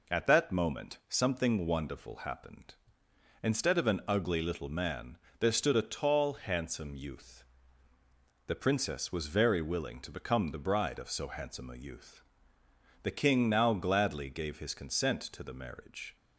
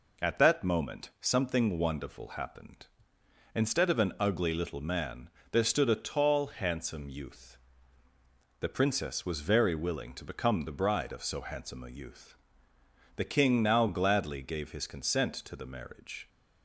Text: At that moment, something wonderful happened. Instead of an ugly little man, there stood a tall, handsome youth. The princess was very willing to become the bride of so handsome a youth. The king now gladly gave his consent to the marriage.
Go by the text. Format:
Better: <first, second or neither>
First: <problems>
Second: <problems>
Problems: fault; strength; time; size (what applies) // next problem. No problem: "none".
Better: neither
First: none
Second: none